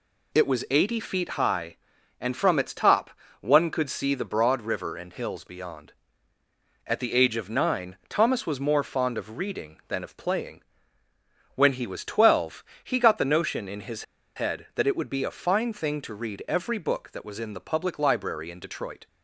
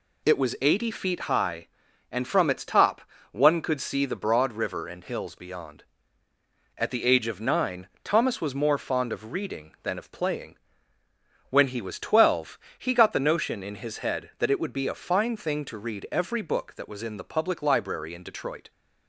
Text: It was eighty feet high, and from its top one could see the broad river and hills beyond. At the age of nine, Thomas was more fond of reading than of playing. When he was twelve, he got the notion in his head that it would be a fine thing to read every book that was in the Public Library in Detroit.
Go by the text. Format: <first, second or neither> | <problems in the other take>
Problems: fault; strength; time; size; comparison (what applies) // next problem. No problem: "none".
second | pauses between "top" and "one"; slight; at 3.0 s; 0.30 s long; slight in the second // pauses between "his" and "head"; slight; at 14.0 s; 0.32 s long